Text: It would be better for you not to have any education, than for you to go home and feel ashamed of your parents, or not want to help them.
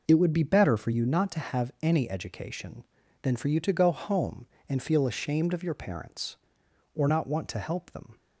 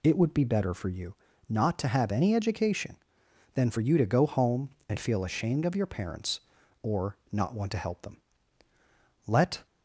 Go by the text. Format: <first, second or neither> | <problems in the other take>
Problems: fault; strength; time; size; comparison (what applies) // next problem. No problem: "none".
first | pauses between "you" and "not"; slight; at 1.1 s; 0.34 s long // pauses between "or" and "not"; slight; at 7.1 s; 0.16 s long // goes on to say "Let"; slight; from 9.2 s on; 0.38 s long